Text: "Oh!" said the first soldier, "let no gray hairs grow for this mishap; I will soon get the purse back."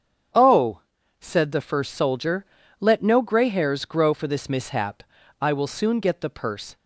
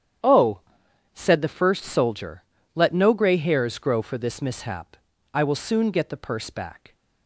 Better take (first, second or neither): second